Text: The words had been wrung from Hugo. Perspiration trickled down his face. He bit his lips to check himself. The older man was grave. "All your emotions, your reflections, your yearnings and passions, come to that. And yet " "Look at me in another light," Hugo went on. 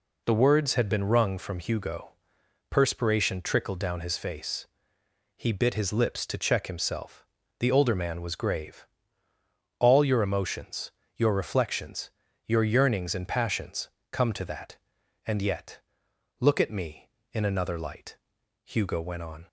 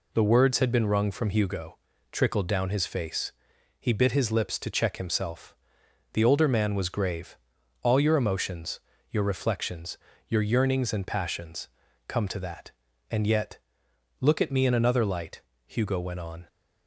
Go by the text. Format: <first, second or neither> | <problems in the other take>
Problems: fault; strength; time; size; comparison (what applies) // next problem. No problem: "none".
first | skips "Perspiration"; at 1.9 s